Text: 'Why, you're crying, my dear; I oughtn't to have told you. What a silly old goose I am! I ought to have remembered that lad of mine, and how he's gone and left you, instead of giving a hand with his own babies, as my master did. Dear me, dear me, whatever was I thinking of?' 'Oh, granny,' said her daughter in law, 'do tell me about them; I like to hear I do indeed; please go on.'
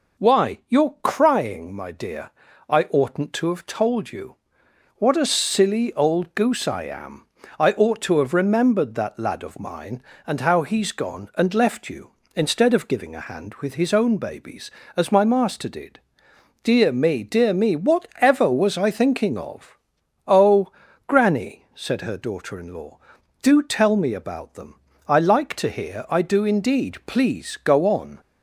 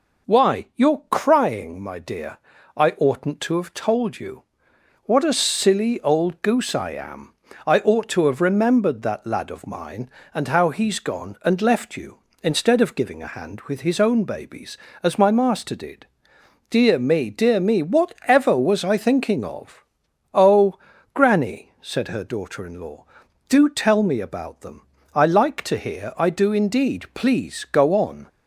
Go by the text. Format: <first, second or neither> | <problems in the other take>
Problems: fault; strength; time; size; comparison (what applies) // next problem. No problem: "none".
neither | none